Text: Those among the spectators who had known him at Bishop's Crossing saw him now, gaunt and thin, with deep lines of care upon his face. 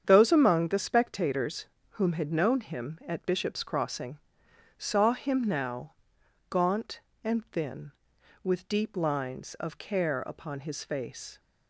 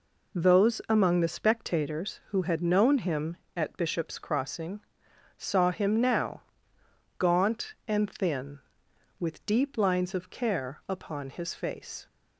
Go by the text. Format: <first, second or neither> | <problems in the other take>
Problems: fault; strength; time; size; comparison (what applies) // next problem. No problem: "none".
second | starts louder than the rest; strong; until 1.0 s; 8 dB // says "whom" for "who"; at 1.8 s // pauses between "Crossing" and "saw"; noticeable; at 4.1 s; 0.58 s long; noticeable in the second